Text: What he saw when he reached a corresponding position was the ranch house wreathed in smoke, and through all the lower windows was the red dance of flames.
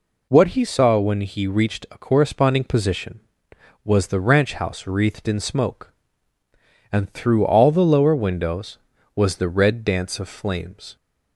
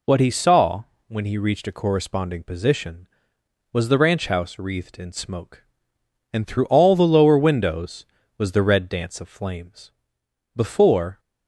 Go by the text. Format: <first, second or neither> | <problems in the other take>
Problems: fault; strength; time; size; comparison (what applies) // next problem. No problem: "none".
first | pauses between "saw" and "when"; slight; at 0.8 s; 0.24 s long // goes on to say "Before"; noticeable; from 10.5 s on; 0.64 s long